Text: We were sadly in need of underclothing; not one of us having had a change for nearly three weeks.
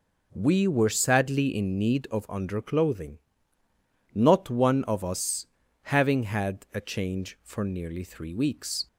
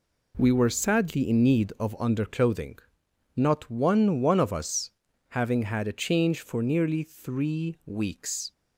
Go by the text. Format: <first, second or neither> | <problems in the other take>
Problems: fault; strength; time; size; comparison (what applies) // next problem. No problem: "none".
first | says "one" twice; at 4.1 s // pauses between "us" and "having"; at 4.8 s; 0.40 s long; also in the first